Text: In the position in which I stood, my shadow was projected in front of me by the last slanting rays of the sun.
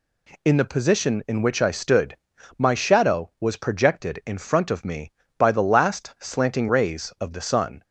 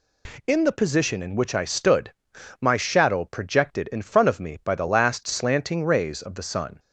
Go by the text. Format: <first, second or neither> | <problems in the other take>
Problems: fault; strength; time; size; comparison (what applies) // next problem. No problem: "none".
first | skips "was"; at 3.2 s